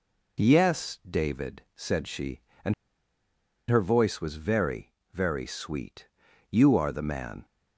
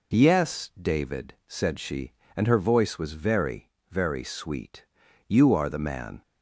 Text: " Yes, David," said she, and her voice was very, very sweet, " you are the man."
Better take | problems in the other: second | pauses between "and" and "her"; noticeable; at 2.7 s; 0.97 s long

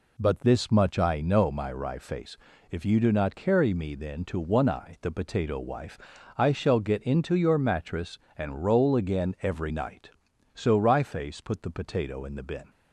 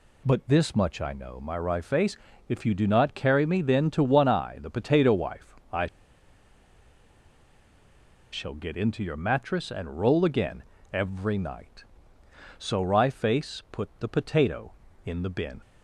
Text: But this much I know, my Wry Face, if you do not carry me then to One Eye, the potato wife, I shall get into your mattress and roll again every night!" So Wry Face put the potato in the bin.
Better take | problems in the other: first | pauses between "I" and "shall"; strong; at 5.8 s; 2.4 s long // pauses between "again" and "every"; slight; at 10.6 s; 0.28 s long

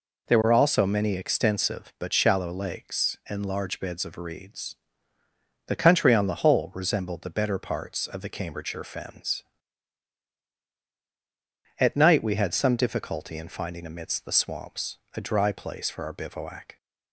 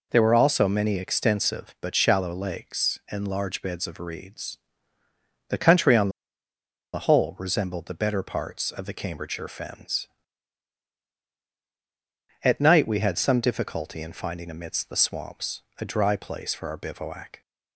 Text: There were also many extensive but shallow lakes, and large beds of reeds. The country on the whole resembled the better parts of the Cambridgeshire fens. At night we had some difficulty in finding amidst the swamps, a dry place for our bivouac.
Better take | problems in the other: first | pauses between "on" and "the"; noticeable; at 6.0 s; 0.84 s long

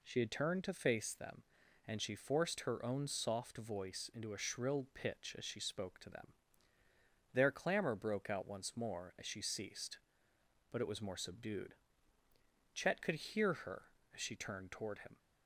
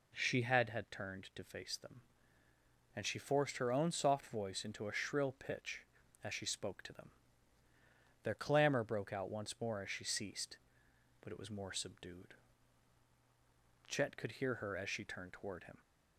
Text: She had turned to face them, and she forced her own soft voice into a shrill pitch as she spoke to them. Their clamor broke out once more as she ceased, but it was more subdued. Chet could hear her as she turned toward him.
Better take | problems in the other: first | says "had" twice; at 0.6 s

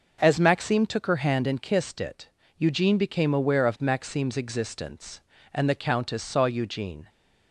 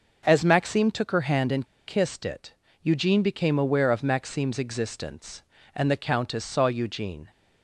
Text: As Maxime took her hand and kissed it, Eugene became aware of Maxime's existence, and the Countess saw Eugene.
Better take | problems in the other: first | pauses between "and" and "kissed"; slight; at 1.6 s; 0.20 s long

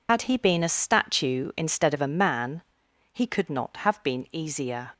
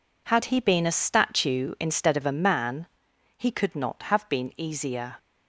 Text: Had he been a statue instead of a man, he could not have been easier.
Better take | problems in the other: second | loses the start of "Had"; at 0.0 s; 65 ms

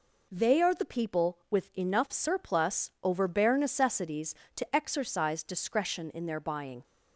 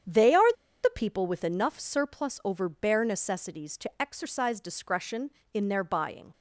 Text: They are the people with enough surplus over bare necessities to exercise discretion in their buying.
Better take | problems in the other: first | starts louder than the rest; strong; until 1.3 s; 8.5 dB // pauses between "are" and "the"; slight; at 0.5 s; 0.30 s long

